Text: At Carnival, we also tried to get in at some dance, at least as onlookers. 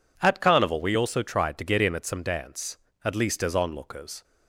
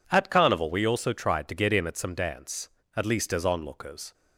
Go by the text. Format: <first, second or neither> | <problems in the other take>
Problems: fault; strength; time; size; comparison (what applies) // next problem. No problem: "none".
neither | none